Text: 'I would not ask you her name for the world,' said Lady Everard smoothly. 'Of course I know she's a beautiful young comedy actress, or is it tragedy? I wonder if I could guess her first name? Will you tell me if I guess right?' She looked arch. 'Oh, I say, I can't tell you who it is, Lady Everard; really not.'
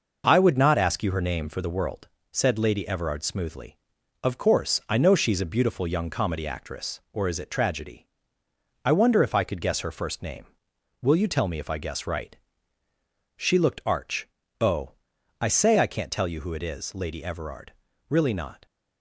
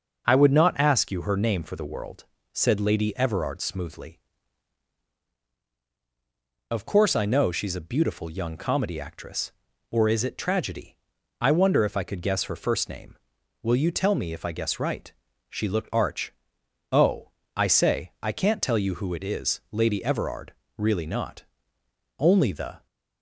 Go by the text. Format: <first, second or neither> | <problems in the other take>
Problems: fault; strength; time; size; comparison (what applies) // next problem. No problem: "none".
first | goes on to say "Only the"; noticeable; from 22.1 s on; 0.68 s long